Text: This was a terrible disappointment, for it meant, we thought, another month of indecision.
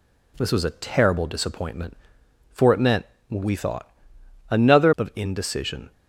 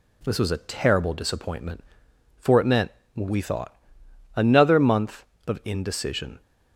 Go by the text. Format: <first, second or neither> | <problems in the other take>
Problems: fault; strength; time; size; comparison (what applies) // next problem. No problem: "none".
second | skips "month"; at 4.9 s